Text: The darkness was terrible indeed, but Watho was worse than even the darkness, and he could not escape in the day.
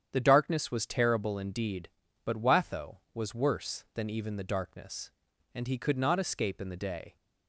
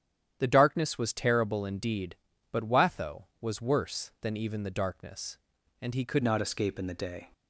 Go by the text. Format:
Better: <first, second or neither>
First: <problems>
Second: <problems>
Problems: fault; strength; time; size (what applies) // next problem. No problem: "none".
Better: first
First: starts louder than the rest; strong; until 1.1 s; 9 dB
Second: starts louder than the rest; strong; until 1.4 s; 10 dB // changes voice at "not"; from 6.2 s on; 1.1 s long